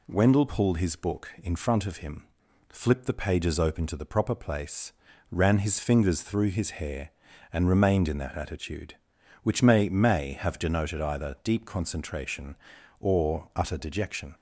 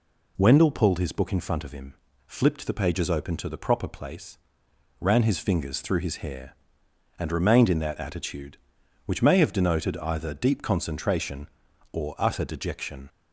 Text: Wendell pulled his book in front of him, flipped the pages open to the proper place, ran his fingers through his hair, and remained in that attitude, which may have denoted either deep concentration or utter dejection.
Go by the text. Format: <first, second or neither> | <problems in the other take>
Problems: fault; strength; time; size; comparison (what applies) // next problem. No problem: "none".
second | says "may" twice; at 9.8 s